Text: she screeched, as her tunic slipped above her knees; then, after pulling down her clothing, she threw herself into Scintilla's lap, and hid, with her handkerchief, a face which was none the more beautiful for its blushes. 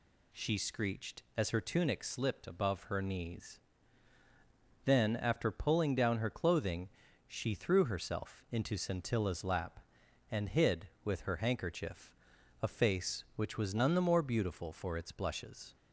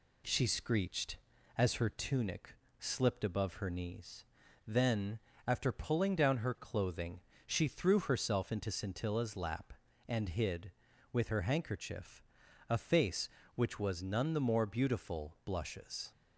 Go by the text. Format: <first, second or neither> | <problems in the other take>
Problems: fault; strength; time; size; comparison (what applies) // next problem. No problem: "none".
first | pauses between "tunic" and "slipped"; slight; at 2.5 s; 0.24 s long // skips "for its"; at 15.4 s